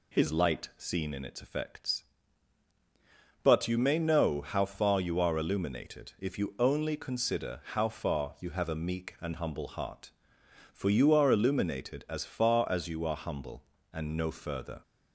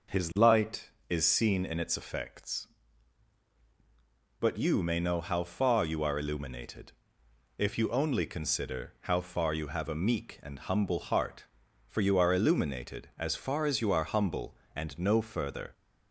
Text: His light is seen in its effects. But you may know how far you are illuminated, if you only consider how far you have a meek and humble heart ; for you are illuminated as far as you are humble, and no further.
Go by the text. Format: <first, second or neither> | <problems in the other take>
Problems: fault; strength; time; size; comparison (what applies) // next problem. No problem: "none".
second | skips "is"; at 0.7 s